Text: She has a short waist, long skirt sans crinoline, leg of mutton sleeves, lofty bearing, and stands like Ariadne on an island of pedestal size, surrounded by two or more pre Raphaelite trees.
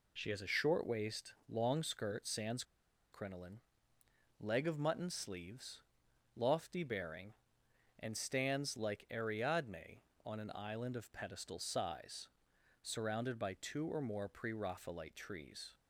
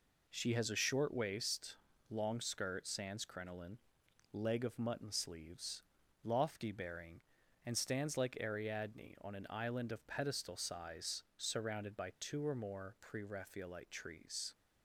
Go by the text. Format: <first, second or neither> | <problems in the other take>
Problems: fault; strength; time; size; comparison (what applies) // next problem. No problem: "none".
second | pauses between "sans" and "crinoline"; noticeable; at 2.6 s; 0.49 s long